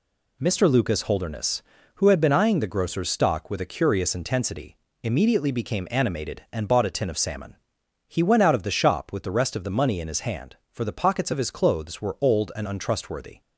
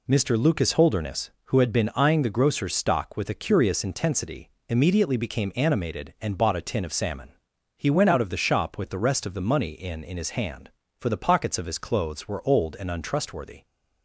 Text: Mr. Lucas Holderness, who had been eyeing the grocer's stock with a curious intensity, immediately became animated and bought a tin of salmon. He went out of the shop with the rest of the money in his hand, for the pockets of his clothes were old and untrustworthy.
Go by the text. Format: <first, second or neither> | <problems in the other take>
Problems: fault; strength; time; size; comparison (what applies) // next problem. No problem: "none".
first | says "in" twice; at 10.0 s